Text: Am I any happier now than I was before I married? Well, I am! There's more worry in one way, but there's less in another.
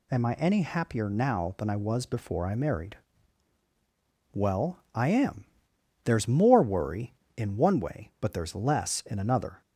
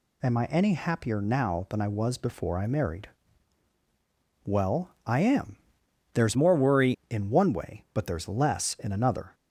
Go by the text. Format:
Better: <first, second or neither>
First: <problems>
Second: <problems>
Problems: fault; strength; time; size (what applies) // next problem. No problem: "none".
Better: first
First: none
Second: changes voice from "more" to "worry"; from 6.3 to 6.9 s; 0.6 s long